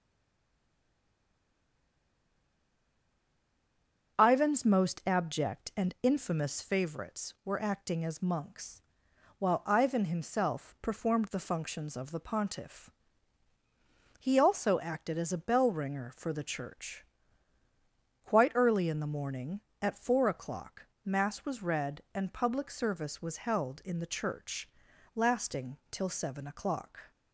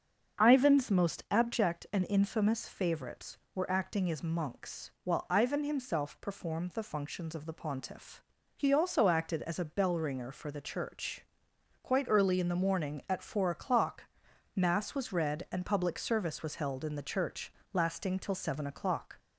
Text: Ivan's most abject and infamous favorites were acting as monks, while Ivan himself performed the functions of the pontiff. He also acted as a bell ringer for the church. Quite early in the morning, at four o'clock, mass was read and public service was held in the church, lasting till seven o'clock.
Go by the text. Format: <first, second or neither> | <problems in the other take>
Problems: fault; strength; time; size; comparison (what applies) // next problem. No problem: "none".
second | stays silent before the first word; strong; until 4.1 s; 4.1 s long // starts louder than the rest; until 5.2 s; 6.5 dB; also in the second